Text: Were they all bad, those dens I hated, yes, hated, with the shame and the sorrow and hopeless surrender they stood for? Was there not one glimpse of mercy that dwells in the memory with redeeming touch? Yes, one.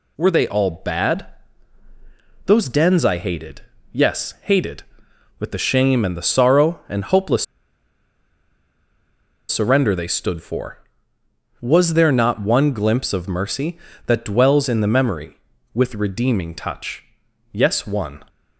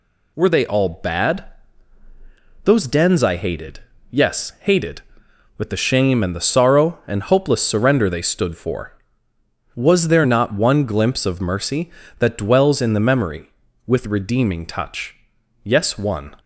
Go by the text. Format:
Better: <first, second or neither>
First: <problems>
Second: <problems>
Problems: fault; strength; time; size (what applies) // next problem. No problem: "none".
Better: second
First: pauses between "hopeless" and "surrender"; strong; at 7.4 s; 2.0 s long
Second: none